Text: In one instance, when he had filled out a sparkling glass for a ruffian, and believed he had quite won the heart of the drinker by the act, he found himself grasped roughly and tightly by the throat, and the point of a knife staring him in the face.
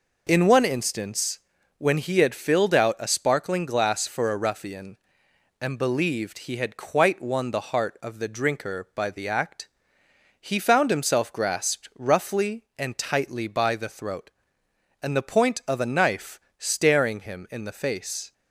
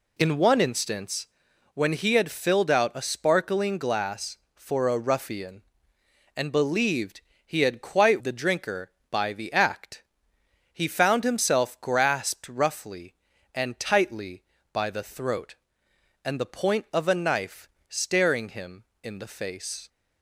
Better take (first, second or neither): first